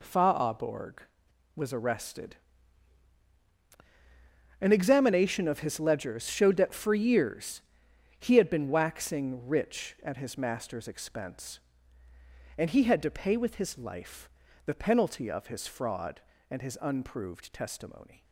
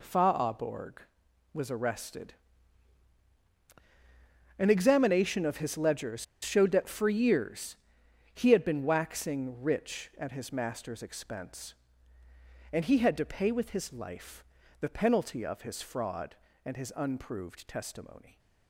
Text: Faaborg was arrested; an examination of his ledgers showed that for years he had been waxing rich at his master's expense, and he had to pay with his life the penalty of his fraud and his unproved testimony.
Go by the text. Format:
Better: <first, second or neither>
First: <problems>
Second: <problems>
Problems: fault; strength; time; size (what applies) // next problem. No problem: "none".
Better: first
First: pauses between "years" and "he"; noticeable; at 7.6 s; 0.56 s long // pauses between "life" and "the"; slight; at 14.2 s; 0.36 s long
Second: pauses between "ledgers" and "showed"; slight; at 6.2 s; 0.19 s long // pauses between "years" and "he"; noticeable; at 7.7 s; 0.56 s long // pauses between "life" and "the"; slight; at 14.4 s; 0.36 s long